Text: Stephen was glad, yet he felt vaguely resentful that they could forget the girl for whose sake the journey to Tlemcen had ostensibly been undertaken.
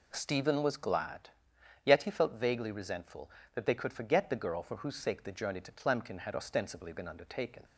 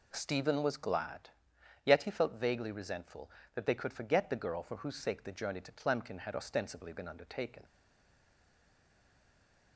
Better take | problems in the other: first | stays silent after the last word; from 7.6 s on; 2.1 s long

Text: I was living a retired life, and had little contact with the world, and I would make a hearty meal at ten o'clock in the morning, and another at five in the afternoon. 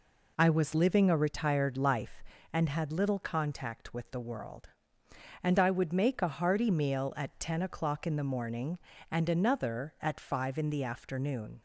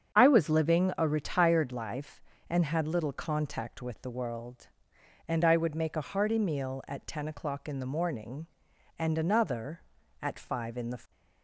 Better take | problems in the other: first | starts louder than the rest; strong; until 1.1 s; 7.5 dB // stops before "afternoon"; at 11.1 s

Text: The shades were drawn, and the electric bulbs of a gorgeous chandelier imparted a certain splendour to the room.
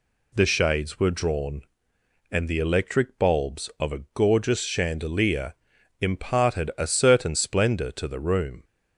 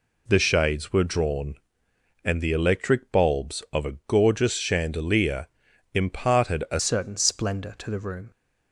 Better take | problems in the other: first | pauses between "chandelier" and "imparted"; noticeable; at 5.4 s; 0.46 s long; noticeable in the first // changes voice at "certain"; from 6.8 s on; 1.5 s long

